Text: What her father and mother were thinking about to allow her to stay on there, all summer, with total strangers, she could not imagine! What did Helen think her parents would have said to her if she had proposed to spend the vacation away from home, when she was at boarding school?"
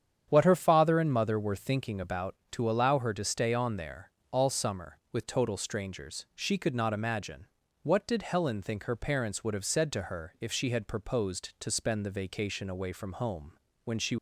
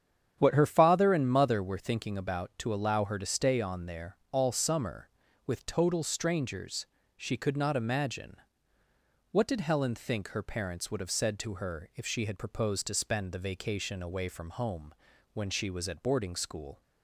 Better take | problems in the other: second | starts louder than the rest; strong; until 1.3 s; 8.5 dB; strong in the second // stops before "was at boarding school"; at 14.1 s

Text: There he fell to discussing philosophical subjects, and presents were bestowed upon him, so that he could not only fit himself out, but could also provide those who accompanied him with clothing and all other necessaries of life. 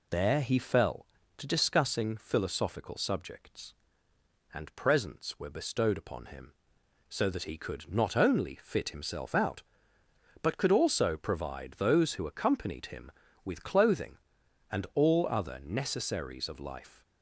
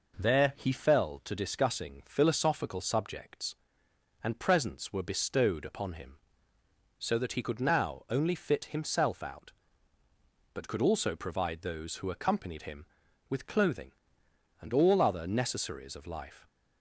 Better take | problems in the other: first | says "now" for "not"; at 7.6 s

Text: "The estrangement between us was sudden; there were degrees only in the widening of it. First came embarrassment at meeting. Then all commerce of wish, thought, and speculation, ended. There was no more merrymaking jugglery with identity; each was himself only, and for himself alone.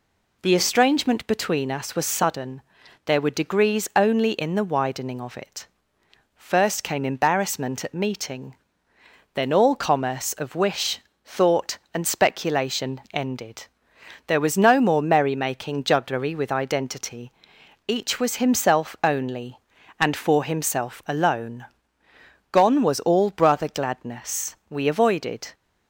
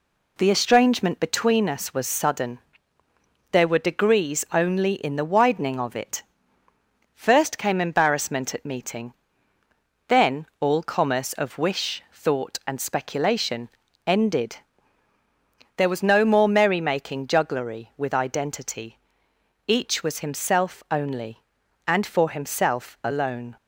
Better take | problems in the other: second | goes on to say "Gone was all brother gladness We avoided"; strong; from 22.5 s on; 3.0 s long

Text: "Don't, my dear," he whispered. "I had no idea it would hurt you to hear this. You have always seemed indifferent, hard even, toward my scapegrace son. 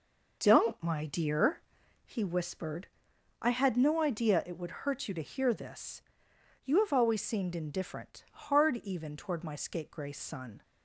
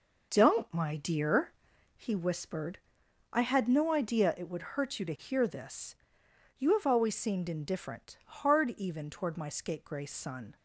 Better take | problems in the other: neither | none

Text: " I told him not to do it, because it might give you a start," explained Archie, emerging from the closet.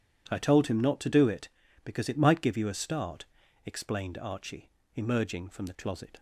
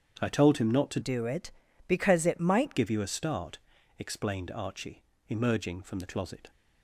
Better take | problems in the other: first | starts louder than the rest; strong; until 1.2 s; 8 dB // changes voice from "do" to "might"; from 1.0 to 2.7 s; 1.7 s long

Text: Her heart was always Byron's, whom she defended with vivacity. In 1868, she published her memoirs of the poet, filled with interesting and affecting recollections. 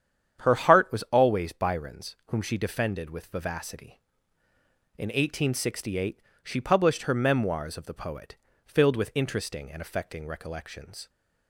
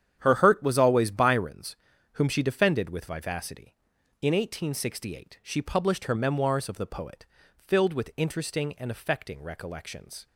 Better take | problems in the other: first | starts louder than the rest; strong; until 1.1 s; 9 dB; strong in the first // says "hurt" for "heart"; at 0.3 s

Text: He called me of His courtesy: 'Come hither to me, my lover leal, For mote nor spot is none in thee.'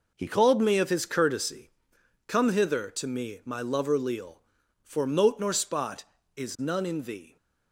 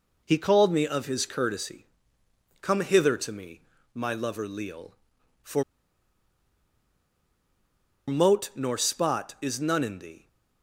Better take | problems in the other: first | pauses between "For" and "mote"; strong; at 5.6 s; 2.4 s long

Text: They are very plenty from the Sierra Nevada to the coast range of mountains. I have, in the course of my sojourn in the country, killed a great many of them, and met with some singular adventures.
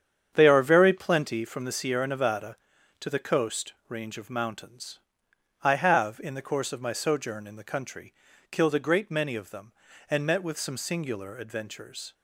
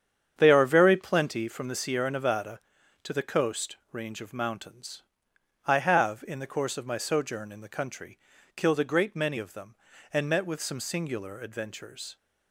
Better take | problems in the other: neither | starts louder than the rest; strong; the same in both

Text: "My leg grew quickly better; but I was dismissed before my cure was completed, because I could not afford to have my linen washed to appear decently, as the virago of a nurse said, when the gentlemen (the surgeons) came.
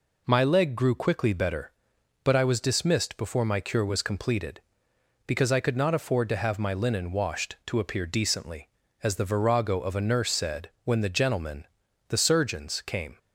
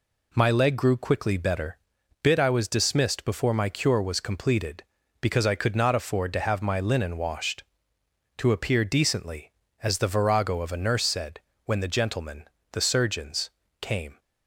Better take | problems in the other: first | says "bit" for "but"; at 2.2 s

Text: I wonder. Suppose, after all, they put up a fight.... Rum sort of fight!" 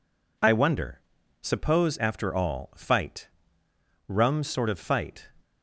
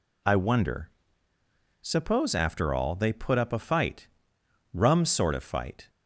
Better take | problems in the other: second | skips "they put up a"; at 2.7 s

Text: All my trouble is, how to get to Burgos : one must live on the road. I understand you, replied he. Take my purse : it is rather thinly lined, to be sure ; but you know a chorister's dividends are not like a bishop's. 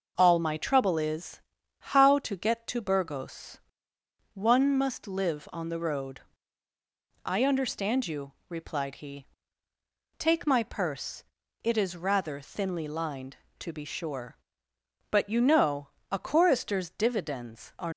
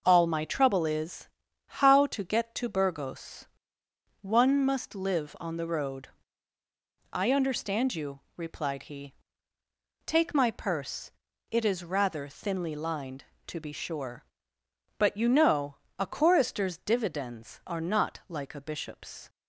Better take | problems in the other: second | pauses between "know" and "a"; slight; at 15.8 s; 0.20 s long; slight in the second // stops before "not like a bishop's"; at 17.9 s

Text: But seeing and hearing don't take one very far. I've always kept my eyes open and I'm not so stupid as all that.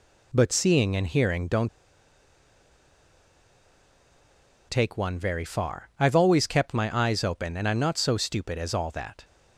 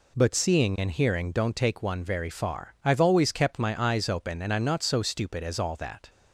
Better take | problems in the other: second | pauses between "don't" and "take"; strong; at 1.6 s; 3.0 s long

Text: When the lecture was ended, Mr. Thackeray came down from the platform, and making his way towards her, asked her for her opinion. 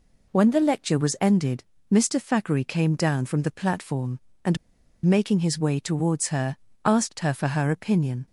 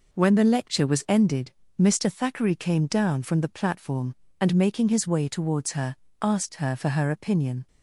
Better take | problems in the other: second | pauses between "and" and "making"; noticeable; at 4.5 s; 0.48 s long

